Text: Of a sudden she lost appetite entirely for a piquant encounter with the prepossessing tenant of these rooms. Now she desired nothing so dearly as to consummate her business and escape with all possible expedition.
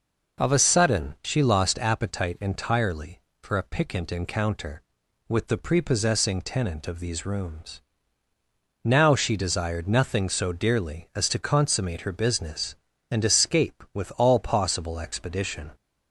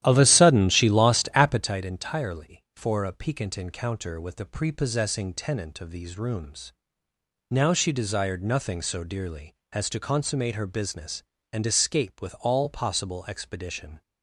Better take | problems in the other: first | starts louder than the rest; strong; until 1.7 s; 12 dB

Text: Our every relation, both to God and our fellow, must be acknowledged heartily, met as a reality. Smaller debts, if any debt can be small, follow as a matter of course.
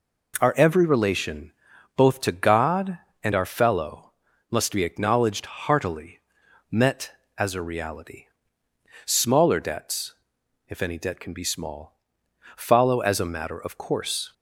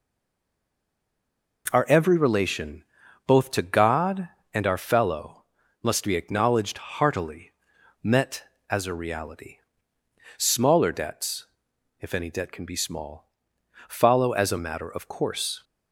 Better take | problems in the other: first | stays silent before the first word; noticeable; until 1.6 s; 1.6 s long

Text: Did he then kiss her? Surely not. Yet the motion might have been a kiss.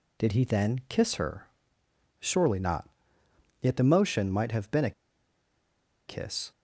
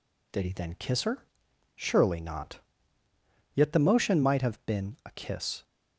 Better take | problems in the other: second | pauses between "a" and "kiss"; at 4.9 s; 1.1 s long

